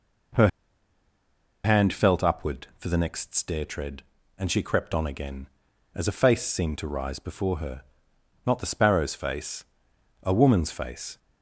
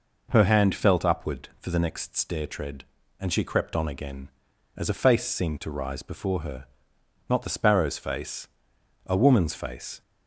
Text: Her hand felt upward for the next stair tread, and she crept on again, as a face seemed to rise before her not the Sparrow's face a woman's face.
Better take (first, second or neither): second